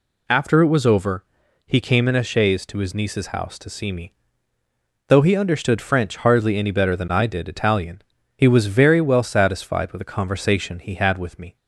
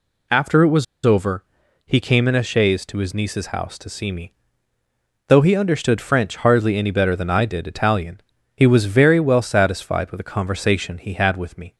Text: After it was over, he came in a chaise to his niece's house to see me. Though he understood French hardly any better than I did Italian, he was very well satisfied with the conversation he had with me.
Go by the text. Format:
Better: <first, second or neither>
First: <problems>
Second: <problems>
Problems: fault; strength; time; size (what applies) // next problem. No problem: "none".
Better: first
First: none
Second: pauses between "was" and "over"; slight; at 0.8 s; 0.19 s long